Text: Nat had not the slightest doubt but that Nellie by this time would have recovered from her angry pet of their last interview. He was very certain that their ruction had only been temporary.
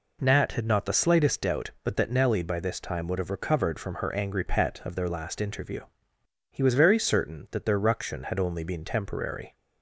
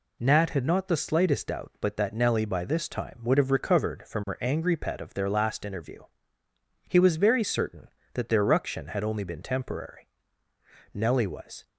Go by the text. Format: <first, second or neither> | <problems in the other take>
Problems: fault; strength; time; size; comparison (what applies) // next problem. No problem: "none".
first | goes on to say "Nellie was"; noticeable; from 10.9 s on; 0.74 s long